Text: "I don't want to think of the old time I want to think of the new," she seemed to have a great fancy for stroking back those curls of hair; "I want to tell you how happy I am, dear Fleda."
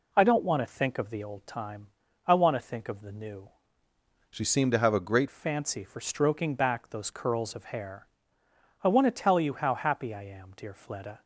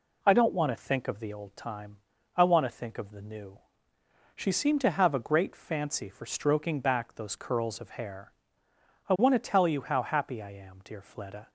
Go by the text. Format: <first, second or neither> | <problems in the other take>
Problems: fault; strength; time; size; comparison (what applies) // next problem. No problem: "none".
second | pauses between "time" and "I"; at 1.8 s; 0.40 s long; also in the second // changes voice from "she" to "great"; from 4.2 to 5.2 s; 1.0 s long